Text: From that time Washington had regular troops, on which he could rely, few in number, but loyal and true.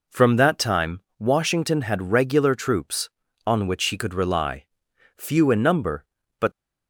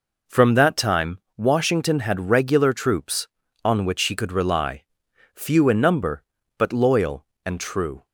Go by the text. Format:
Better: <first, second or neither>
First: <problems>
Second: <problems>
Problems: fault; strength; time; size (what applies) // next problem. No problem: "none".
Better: second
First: pauses between "time" and "Washington"; slight; at 0.9 s; 0.18 s long // stops before "loyal and true"; at 6.5 s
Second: pauses between "time" and "Washington"; slight; at 1.1 s; 0.18 s long